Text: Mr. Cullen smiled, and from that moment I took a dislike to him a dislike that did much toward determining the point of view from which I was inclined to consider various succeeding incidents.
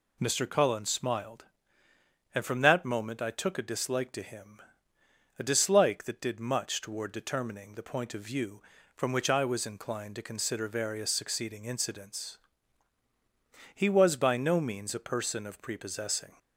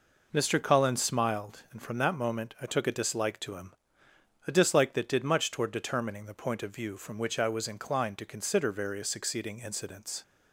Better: second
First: pauses between "him" and "a"; noticeable; at 4.5 s; 0.80 s long // goes on to say "He was by no means a person of prepossessing"; strong; from 13.7 s on; 2.6 s long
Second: pauses between "him" and "a"; noticeable; at 3.7 s; 0.72 s long

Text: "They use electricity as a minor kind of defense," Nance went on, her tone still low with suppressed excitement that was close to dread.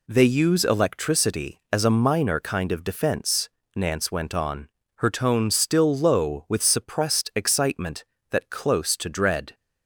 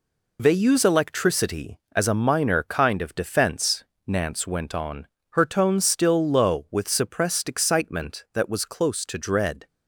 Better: second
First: skips "was"; at 8.5 s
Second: none

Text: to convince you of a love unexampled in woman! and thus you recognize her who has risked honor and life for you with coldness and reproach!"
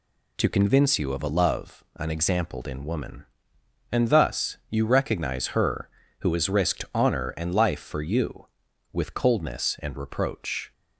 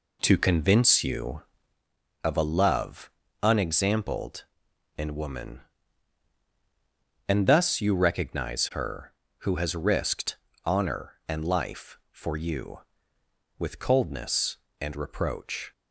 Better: first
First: none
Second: starts louder than the rest; until 1.8 s; 3.5 dB // pauses between "love" and "unexampled"; slight; at 3.1 s; 0.32 s long // pauses between "risked" and "honor"; slight; at 10.3 s; 0.28 s long

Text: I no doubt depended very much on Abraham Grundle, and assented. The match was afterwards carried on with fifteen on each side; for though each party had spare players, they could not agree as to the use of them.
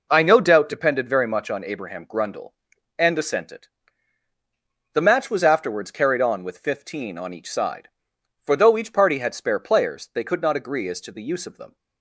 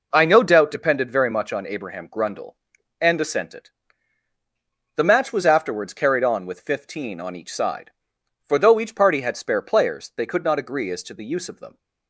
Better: neither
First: none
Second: none

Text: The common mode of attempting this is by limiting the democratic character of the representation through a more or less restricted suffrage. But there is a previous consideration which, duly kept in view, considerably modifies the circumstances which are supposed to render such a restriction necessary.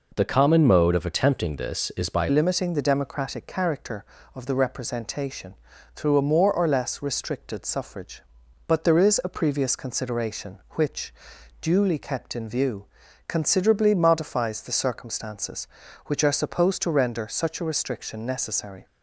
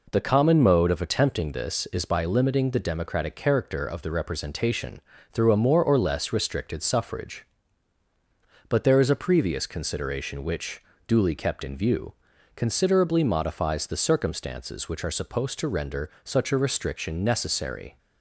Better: second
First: changes voice at "limiting"; from 2.2 s on; 16.6 s long // pauses between "representation" and "through"; at 5.5 s; 0.40 s long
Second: pauses between "representation" and "through"; slight; at 5.0 s; 0.32 s long

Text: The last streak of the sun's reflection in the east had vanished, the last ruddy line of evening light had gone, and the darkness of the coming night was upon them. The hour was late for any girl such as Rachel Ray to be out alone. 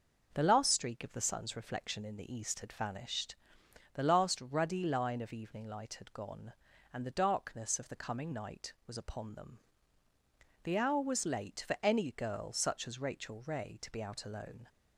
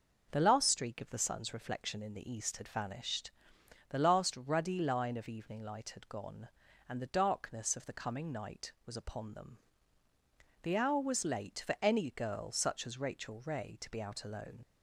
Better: first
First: none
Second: leaves "alone" unfinished; at 14.6 s; 40 ms

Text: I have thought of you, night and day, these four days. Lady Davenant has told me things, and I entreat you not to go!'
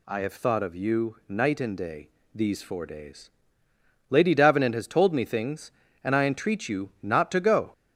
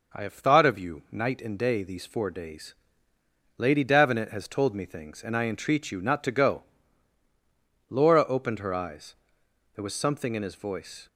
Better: first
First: none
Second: goes on to say "Laura opened her eyes there was something in his voice"; strong; from 7.8 s on; 3.1 s long

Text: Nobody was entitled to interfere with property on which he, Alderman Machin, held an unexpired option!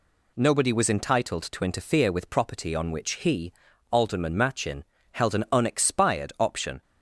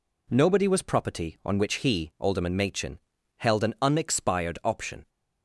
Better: first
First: none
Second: skips "entitled to interfere with"; at 0.8 s

